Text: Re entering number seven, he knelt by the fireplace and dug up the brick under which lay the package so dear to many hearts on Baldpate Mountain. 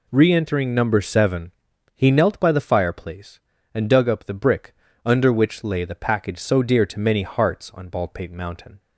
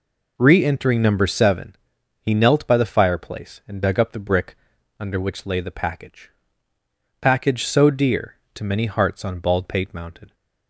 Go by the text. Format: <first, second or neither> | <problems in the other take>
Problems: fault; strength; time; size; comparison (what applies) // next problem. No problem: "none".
first | pauses between "brick" and "under"; at 4.5 s; 0.42 s long; slight in the first // says "package" twice; at 7.1 s